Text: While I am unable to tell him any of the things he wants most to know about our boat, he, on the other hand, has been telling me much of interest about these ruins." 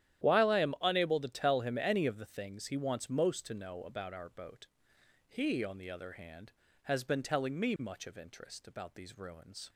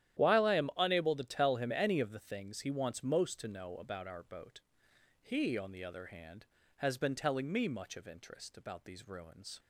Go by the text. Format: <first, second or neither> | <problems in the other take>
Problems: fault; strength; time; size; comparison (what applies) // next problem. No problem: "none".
neither | starts louder than the rest; strong; the same in both